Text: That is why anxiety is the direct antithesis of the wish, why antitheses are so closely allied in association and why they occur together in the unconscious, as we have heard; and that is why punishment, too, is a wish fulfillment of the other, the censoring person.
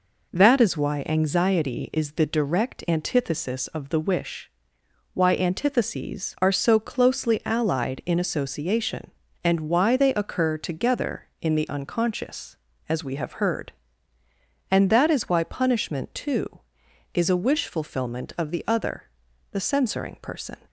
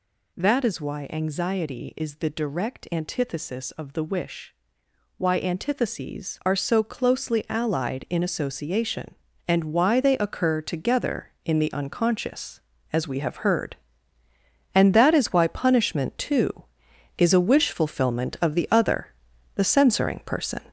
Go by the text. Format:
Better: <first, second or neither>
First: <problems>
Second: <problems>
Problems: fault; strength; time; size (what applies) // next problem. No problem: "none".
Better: first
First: none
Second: gets louder; strong; throughout; 7 dB